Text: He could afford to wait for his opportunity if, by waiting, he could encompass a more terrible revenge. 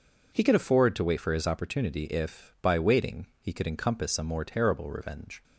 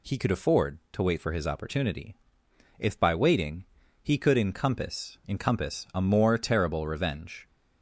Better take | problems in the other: first | pauses between "opportunity" and "if"; noticeable; at 2.1 s; 0.62 s long // says "encompass" twice; at 5.2 s

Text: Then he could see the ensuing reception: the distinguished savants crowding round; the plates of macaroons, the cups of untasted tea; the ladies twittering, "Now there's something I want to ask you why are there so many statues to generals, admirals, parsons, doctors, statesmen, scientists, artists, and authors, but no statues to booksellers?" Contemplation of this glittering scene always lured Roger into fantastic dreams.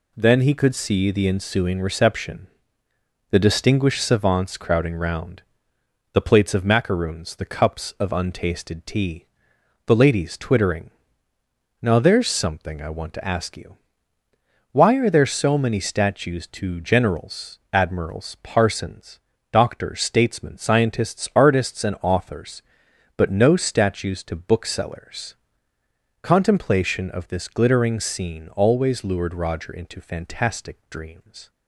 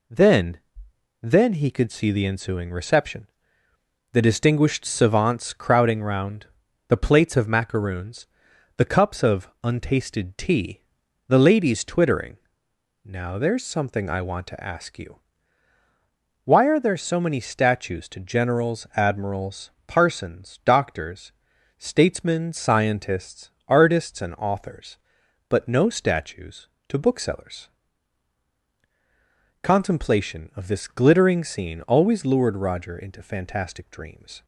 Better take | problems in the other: first | says "Then" twice; at 1.2 s // pauses between "of" and "untasted"; slight; at 9.4 s; 0.16 s long // pauses between "you" and "why"; strong; at 15.1 s; 1.2 s long; noticeable in the first

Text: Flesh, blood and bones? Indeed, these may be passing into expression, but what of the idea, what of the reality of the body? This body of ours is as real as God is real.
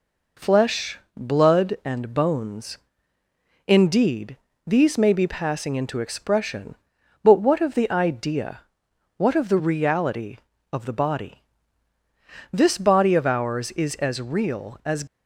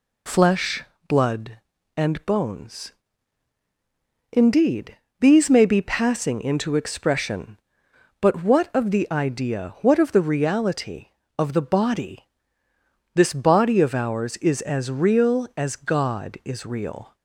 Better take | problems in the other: second | stops before "God is real"; at 15.0 s

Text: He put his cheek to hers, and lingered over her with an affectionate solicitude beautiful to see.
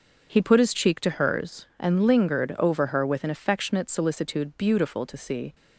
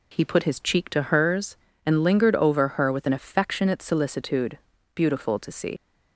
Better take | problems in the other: first | pauses between "solicitude" and "beautiful"; slight; at 4.5 s; 0.36 s long // leaves "see" unfinished; at 5.7 s; 95 ms

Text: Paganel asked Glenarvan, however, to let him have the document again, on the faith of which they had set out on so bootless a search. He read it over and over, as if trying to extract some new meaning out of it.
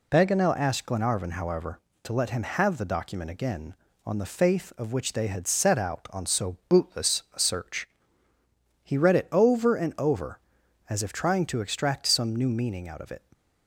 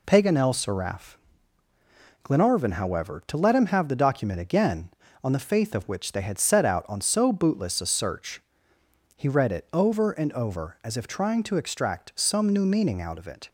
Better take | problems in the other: first | says "seraph" for "asked"; at 0.5 s

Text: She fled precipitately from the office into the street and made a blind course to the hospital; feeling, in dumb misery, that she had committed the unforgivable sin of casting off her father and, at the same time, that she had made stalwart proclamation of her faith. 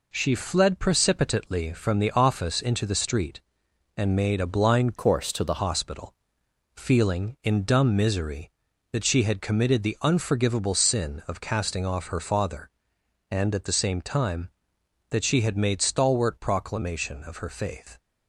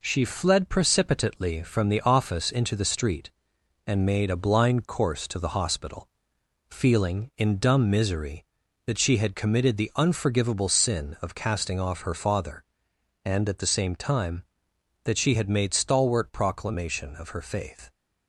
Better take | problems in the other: second | changes voice from "course" to "the"; from 4.9 to 5.5 s; 0.6 s long

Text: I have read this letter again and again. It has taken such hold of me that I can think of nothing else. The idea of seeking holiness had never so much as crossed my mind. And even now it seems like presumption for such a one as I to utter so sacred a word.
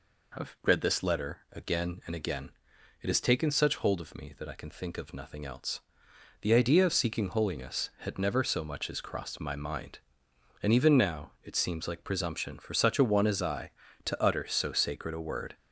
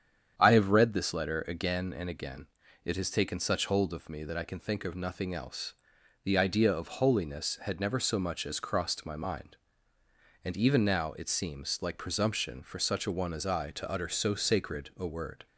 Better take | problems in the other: first | starts louder than the rest; strong; until 1.3 s; 8.5 dB // skips "seeking"; at 6.8 s

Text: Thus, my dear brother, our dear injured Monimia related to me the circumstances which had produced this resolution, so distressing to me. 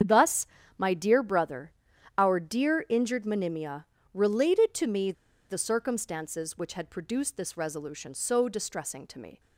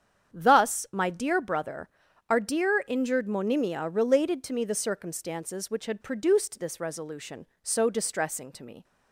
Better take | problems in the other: second | starts louder than the rest; strong; until 1.3 s; 8 dB; strong in the second // pauses between "Monimia" and "related"; slight; at 3.8 s; 0.28 s long // pauses between "me" and "the"; at 5.1 s; 0.37 s long

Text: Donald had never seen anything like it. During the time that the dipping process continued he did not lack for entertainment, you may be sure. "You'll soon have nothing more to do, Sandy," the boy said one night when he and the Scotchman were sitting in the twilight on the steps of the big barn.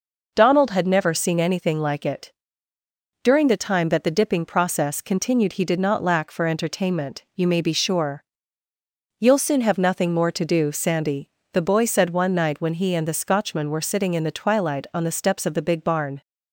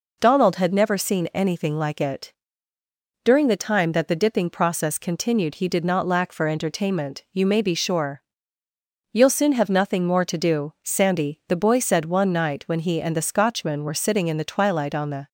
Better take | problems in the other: first | stops before "steps of the big barn"; at 15.2 s

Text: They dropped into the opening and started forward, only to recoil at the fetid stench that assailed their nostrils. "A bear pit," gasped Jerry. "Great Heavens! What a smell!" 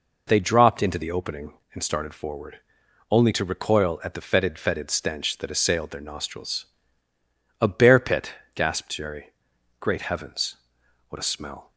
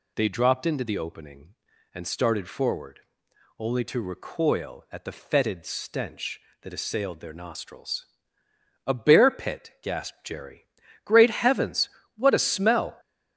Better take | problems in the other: second | says "fetid" twice; at 4.5 s

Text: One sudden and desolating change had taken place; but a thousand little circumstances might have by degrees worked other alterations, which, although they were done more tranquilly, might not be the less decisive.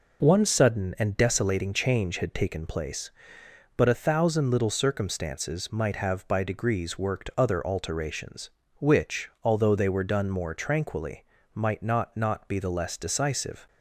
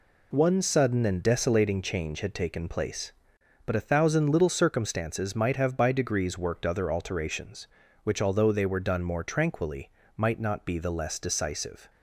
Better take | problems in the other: second | says "not" twice; at 12.1 s

